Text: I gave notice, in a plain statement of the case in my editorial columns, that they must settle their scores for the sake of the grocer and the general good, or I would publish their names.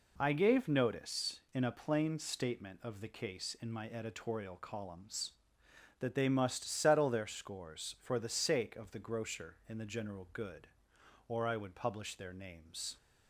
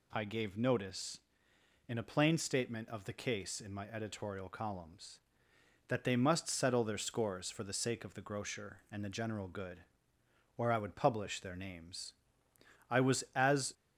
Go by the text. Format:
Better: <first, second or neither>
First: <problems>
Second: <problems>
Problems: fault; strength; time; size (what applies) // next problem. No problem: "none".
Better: first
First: none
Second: goes on to say "I was as"; noticeable; from 12.8 s on; 0.84 s long